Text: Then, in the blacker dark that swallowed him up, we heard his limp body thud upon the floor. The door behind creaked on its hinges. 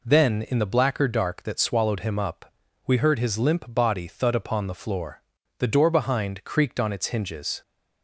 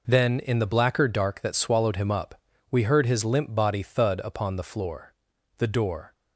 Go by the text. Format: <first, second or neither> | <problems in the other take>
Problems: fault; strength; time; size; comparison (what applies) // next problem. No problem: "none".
first | stops before "behind creaked on its hinges"; at 6.1 s